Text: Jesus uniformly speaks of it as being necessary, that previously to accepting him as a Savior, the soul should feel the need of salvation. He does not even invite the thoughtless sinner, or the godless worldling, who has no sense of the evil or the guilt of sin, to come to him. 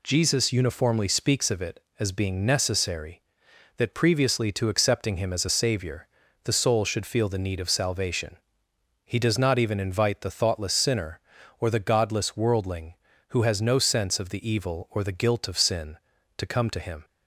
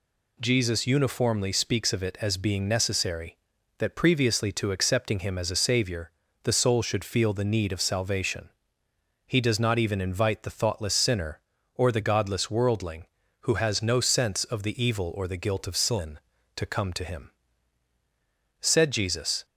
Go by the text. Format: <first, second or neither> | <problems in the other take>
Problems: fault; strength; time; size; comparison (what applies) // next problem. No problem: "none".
first | goes on to say "Said Jesus"; noticeable; from 18.6 s on; 0.84 s long